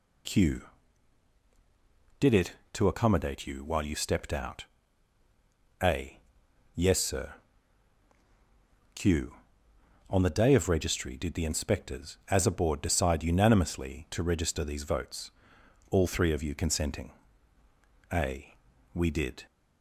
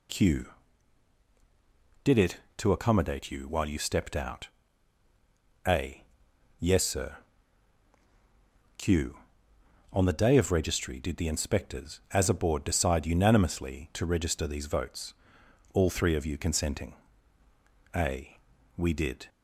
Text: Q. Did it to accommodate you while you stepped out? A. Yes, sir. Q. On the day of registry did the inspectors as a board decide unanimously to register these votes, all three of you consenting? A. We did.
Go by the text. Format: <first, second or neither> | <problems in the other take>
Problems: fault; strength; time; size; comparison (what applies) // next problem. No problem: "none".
neither | none